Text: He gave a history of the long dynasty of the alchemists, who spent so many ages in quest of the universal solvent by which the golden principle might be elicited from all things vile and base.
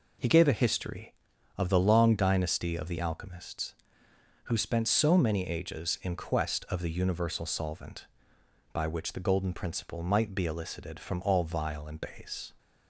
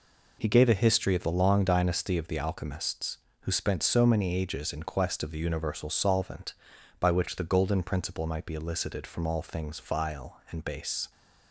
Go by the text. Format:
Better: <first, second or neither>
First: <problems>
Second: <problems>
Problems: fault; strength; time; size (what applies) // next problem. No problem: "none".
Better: second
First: skips "things"; at 11.4 s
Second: none